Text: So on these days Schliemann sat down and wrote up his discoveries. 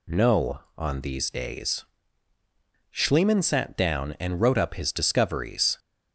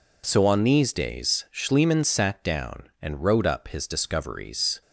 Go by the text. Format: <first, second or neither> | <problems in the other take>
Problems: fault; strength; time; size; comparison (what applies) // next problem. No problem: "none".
second | says "No" for "So"; at 0.0 s // pauses between "days" and "Schliemann"; at 1.8 s; 1.0 s long